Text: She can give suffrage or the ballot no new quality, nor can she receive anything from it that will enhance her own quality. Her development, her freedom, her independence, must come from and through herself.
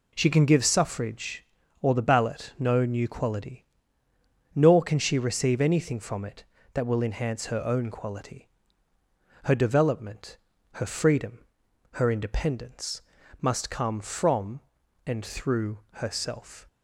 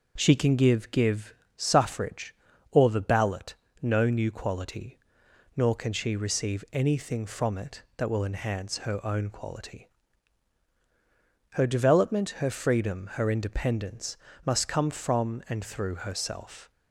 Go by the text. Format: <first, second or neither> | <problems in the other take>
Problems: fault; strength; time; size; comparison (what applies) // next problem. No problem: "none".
first | says "give" twice; at 0.9 s // pauses between "ballot" and "no"; slight; at 3.5 s; 0.28 s long